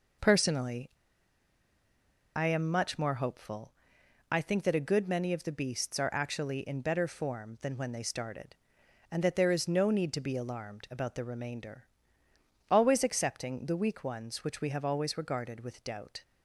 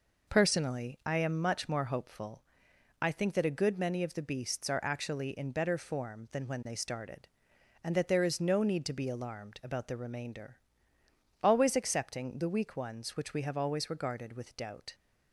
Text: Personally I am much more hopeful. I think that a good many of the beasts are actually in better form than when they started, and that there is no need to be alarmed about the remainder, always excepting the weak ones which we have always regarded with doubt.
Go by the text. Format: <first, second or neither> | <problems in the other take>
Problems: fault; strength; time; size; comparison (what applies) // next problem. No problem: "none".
second | pauses between "Personally" and "I"; strong; at 0.8 s; 1.4 s long